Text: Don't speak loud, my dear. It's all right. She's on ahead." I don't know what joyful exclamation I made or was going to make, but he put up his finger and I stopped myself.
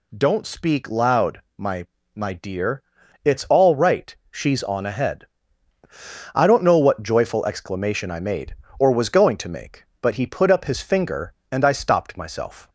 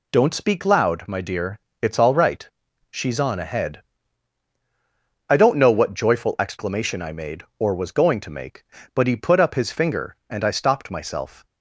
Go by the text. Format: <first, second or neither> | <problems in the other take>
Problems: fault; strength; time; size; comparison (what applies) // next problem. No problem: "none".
second | says "my" twice; at 2.1 s